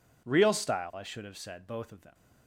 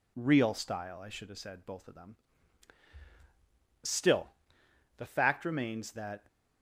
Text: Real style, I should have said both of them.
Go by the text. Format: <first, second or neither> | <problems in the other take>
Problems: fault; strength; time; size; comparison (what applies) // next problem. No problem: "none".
first | goes on to say "Still the fact remains that"; strong; from 3.8 s on; 2.4 s long